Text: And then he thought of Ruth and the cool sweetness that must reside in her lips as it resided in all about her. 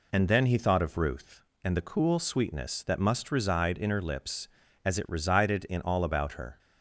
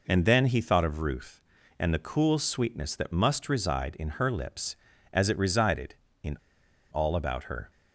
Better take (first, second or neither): first